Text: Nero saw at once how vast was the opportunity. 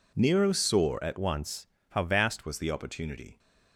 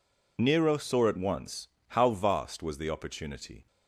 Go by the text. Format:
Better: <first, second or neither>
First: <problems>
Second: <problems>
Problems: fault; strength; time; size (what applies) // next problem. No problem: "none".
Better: second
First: changes voice from "once" to "vast"; from 1.1 to 2.4 s; 1.3 s long // pauses between "once" and "how"; slight; at 1.6 s; 0.24 s long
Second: pauses between "once" and "how"; slight; at 1.6 s; 0.20 s long